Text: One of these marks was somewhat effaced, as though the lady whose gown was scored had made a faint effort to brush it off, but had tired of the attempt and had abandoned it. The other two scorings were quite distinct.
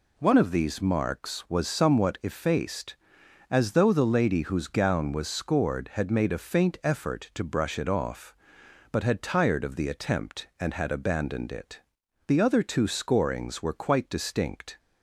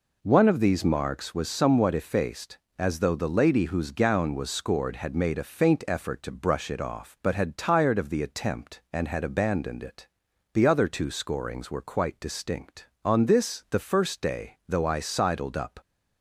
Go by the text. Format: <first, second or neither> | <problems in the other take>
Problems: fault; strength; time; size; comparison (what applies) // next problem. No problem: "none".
first | goes on to say "On this the first day though I sidled up"; strong; from 13.0 s on; 2.7 s long